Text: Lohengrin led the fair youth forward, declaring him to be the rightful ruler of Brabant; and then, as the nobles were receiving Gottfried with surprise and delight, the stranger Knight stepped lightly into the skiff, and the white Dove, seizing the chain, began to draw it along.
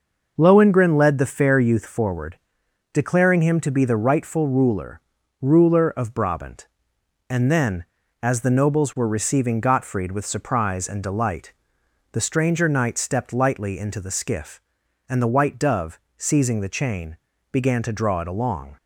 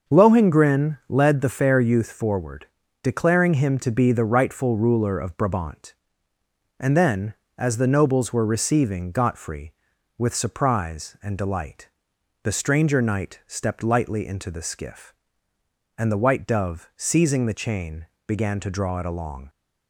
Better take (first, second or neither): second